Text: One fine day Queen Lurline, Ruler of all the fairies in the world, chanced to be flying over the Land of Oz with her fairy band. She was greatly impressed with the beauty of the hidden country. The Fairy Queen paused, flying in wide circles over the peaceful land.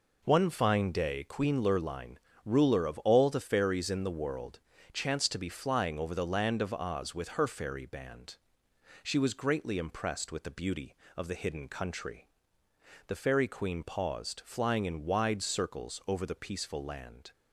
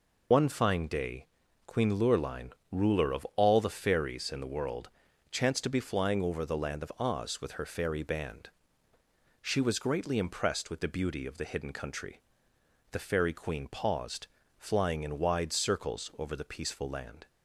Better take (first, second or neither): first